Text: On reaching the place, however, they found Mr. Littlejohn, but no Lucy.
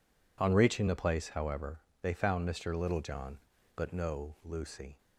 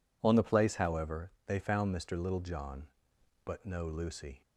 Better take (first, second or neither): first